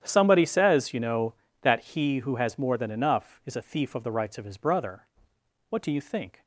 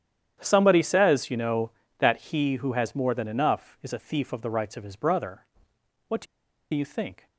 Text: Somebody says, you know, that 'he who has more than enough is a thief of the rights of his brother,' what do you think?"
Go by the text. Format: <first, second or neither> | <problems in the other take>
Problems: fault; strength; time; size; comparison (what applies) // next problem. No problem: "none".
first | starts louder than the rest; strong; until 1.4 s; 10 dB; strong in the first // pauses between "do" and "you"; noticeable; at 6.2 s; 0.48 s long